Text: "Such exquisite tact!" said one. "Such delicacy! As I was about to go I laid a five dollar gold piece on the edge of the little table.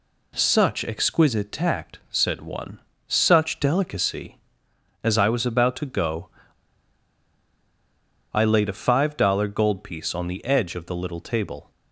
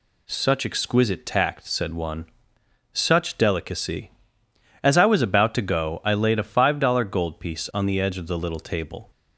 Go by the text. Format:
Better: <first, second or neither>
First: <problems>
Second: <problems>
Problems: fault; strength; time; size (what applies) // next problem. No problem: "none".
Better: second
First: pauses between "go" and "I"; strong; at 6.2 s; 2.0 s long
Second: none